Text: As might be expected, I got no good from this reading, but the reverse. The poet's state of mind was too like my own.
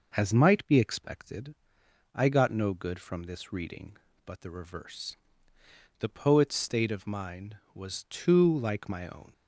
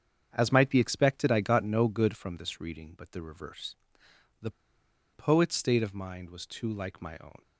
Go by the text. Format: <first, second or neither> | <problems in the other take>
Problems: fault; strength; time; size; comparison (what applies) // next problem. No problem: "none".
first | starts louder than the rest; strong; until 1.3 s; 7.5 dB // pauses between "The" and "poet's"; noticeable; at 4.5 s; 0.63 s long